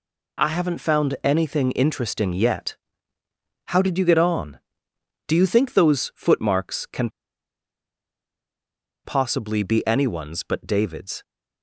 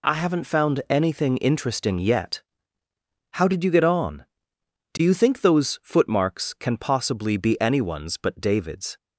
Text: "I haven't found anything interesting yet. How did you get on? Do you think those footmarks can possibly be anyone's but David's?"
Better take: second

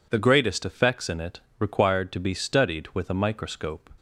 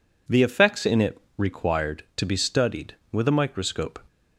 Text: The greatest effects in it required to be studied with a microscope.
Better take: first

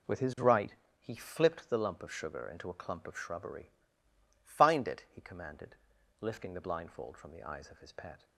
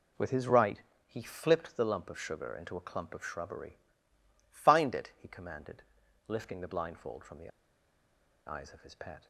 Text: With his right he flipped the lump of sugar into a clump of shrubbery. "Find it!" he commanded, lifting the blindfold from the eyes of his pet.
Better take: first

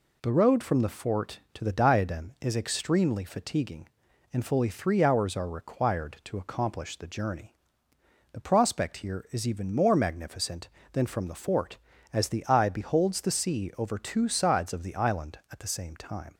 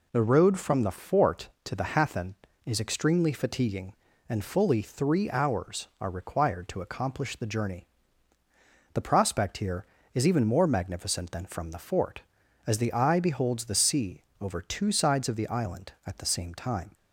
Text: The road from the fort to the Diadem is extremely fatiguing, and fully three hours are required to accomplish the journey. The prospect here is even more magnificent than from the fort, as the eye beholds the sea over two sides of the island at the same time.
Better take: first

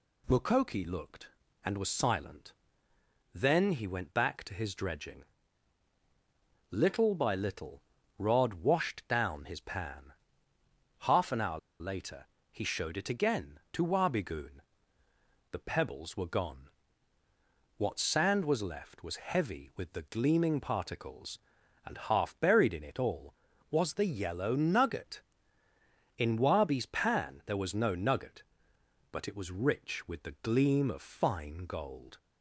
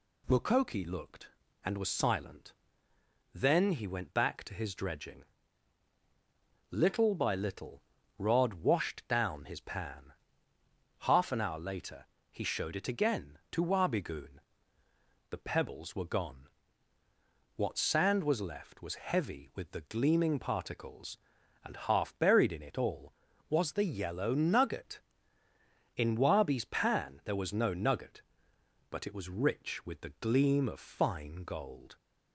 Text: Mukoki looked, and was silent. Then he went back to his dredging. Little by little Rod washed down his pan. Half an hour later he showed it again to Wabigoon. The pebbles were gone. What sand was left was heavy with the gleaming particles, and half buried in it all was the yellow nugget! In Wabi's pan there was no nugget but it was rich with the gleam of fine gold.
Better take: second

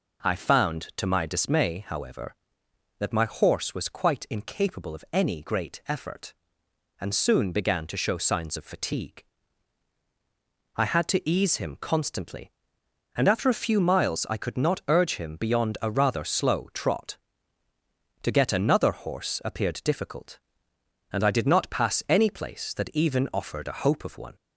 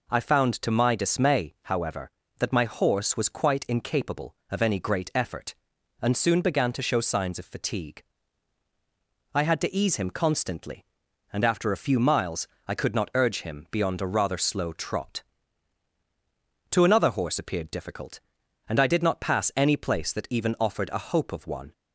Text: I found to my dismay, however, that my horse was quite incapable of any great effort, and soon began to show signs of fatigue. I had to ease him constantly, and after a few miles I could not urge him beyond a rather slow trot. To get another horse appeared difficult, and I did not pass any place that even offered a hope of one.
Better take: first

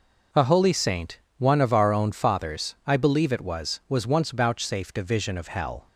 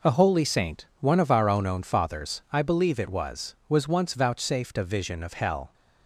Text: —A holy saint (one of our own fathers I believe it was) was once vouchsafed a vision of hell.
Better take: first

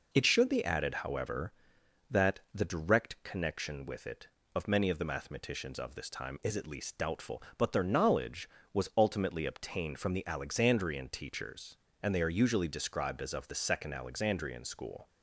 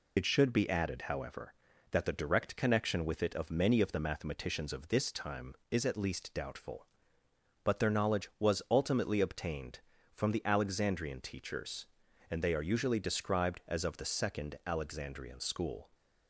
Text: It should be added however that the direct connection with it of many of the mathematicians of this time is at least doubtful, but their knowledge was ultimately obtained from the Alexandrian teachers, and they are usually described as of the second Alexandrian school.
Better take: first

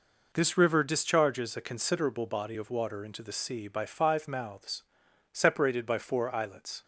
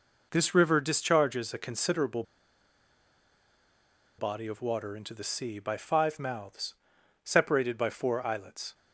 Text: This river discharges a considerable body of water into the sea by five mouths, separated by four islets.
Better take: first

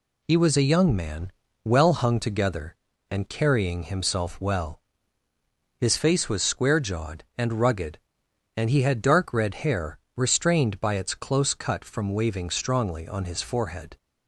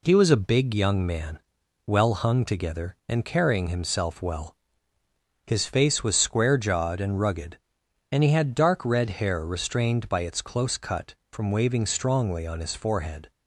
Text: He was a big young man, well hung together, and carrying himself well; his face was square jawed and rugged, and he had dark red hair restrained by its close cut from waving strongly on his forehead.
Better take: second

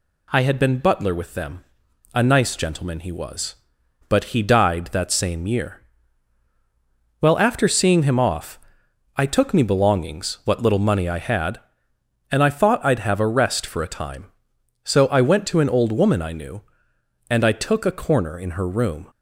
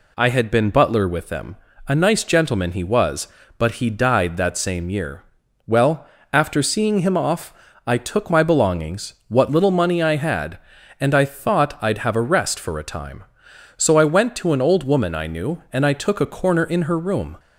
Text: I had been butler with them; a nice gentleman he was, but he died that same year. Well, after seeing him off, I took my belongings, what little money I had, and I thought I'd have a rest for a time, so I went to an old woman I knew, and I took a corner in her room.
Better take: second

